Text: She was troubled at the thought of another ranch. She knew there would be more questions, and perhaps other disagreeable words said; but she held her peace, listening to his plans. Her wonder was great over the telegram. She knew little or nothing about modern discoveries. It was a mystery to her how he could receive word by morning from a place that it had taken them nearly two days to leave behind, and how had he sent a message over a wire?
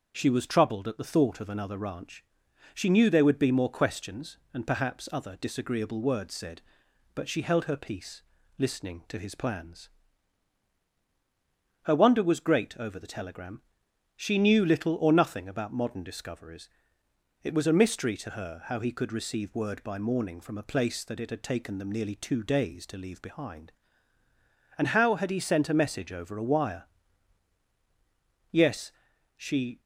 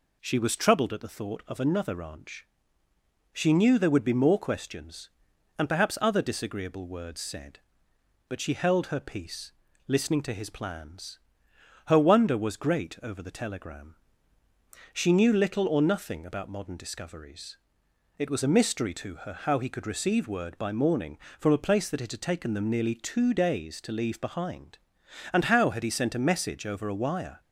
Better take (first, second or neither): second